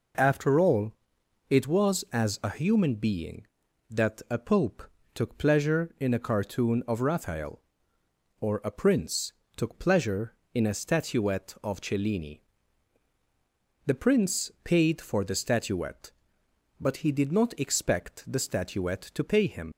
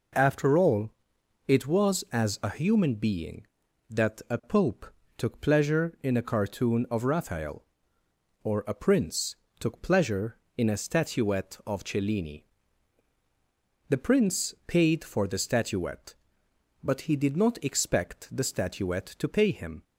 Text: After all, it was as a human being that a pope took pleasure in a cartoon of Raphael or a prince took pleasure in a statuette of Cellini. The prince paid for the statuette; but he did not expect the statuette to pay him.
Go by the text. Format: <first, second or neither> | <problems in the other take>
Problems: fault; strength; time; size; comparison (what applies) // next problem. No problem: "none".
second | pauses between "pope" and "took"; slight; at 4.8 s; 0.30 s long; slight in the second // pauses between "prince" and "took"; slight; at 9.3 s; 0.24 s long; slight in the second // leaves "him" unfinished; at 19.7 s; 65 ms